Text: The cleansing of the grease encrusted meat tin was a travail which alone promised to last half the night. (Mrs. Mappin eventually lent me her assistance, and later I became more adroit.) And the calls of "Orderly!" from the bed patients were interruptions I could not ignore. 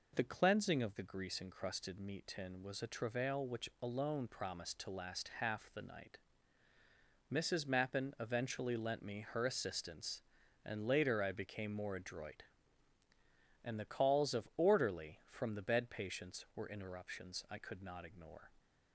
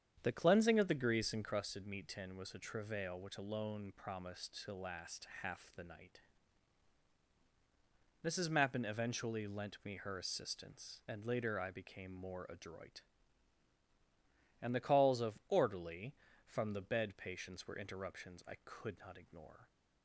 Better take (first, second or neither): first